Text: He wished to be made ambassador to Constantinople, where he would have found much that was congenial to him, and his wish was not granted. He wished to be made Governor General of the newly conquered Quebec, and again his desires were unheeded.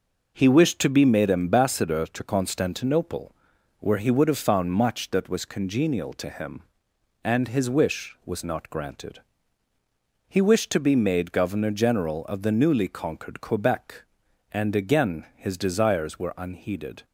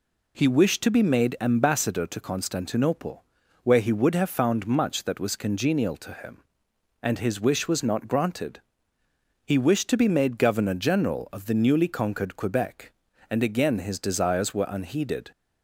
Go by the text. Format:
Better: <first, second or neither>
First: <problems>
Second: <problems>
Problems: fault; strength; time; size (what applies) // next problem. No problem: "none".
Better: neither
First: none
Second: none